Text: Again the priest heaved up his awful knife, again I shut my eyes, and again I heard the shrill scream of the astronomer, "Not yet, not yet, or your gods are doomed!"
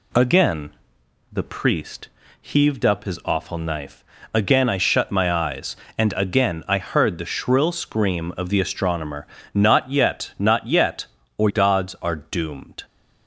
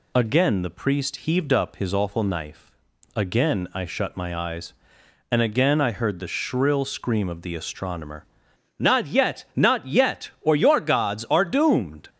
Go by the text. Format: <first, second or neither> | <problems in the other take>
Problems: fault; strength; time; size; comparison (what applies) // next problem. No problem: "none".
second | pauses between "Again" and "the"; noticeable; at 0.7 s; 0.58 s long // pauses between "priest" and "heaved"; slight; at 2.0 s; 0.30 s long // skips "your"; at 11.4 s